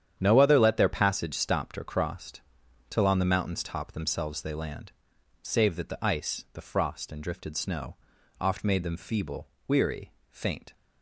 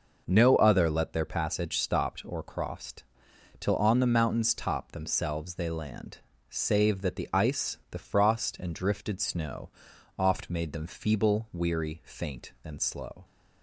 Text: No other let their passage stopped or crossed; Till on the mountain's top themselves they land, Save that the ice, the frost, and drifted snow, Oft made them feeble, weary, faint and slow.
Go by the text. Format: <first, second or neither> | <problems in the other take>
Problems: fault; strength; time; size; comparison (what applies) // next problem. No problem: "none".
second | starts louder than the rest; strong; until 1.1 s; 9 dB // stops before "and slow"; at 10.7 s